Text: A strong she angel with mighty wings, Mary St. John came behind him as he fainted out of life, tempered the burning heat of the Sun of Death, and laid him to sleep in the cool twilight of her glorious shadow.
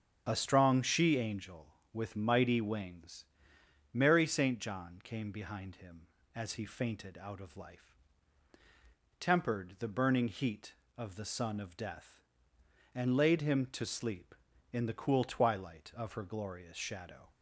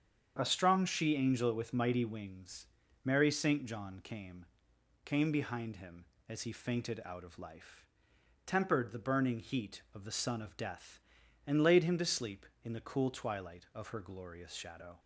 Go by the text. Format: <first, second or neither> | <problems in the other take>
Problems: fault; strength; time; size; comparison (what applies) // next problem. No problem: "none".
first | starts louder than the rest; strong; until 1.4 s; 7.5 dB; strong in the first // says "came" twice; at 5.0 s